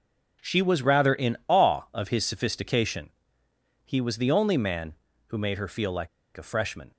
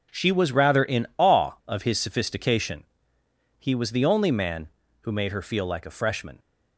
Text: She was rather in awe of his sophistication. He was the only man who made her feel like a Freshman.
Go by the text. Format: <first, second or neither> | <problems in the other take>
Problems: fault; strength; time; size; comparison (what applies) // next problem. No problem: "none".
second | pauses between "like" and "a"; slight; at 6.0 s; 0.28 s long